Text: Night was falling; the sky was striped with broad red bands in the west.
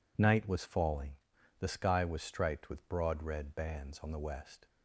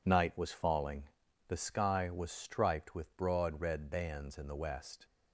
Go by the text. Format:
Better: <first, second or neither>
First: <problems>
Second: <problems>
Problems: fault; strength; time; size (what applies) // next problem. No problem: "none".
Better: second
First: says "on" for "in"; at 3.9 s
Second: none